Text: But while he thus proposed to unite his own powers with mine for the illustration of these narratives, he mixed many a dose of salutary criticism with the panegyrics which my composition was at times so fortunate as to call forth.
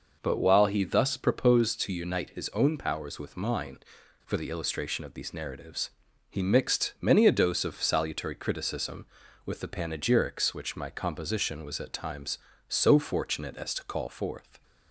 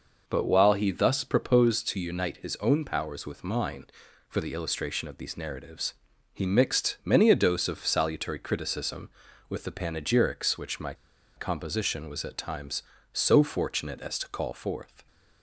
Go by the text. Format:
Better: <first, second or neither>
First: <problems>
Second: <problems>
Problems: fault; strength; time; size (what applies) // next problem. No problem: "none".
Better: first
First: none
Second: pauses between "my" and "composition"; at 10.9 s; 0.42 s long